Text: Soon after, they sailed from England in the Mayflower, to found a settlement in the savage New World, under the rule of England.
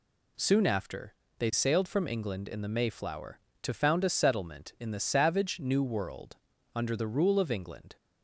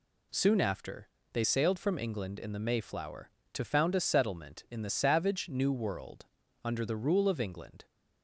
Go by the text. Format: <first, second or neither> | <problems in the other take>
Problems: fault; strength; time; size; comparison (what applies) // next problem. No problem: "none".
neither | none